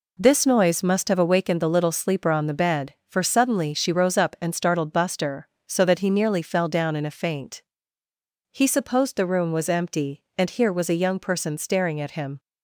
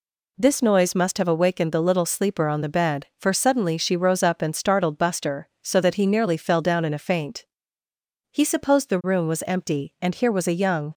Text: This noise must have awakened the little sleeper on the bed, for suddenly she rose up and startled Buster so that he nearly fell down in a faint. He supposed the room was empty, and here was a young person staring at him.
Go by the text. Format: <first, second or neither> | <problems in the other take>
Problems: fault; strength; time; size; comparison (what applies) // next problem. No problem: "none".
first | stops before "person staring at him"; at 10.9 s